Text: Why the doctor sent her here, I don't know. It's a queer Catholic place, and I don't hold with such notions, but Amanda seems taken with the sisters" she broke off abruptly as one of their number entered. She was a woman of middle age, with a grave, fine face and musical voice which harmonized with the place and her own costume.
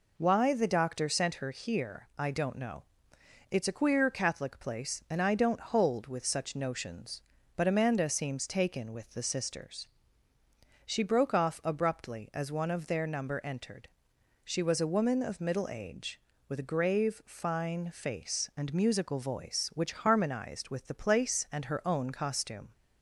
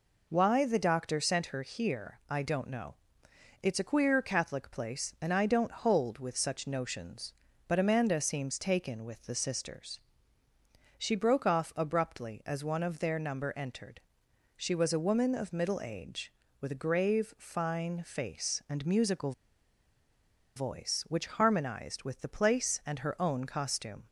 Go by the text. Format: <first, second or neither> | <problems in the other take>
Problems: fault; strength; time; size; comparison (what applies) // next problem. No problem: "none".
first | pauses between "sisters" and "she"; noticeable; at 9.9 s; 0.98 s long; noticeable in the first // pauses between "musical" and "voice"; strong; at 19.3 s; 1.2 s long